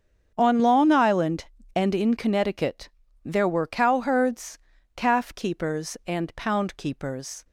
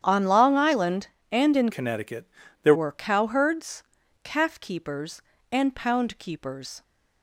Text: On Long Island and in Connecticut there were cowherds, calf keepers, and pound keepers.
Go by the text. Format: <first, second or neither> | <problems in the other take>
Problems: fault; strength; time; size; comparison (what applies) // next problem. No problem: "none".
first | starts louder than the rest; strong; until 1.0 s; 9 dB; strong in the first // changes voice from "Connecticut" to "there"; from 1.7 to 2.7 s; 1.0 s long // pauses between "Connecticut" and "there"; at 2.2 s; 0.40 s long; slight in the first